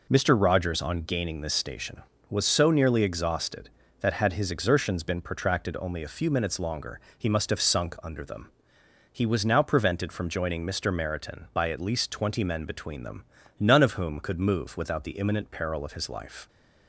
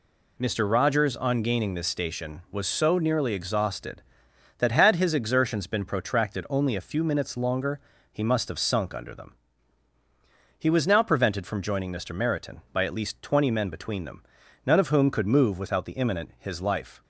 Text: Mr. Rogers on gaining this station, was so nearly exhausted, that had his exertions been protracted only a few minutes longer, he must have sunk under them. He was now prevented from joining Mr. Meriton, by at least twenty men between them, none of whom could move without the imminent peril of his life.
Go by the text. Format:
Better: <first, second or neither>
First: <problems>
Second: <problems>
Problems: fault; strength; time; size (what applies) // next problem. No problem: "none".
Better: first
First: none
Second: skips "peril of"; at 16.3 s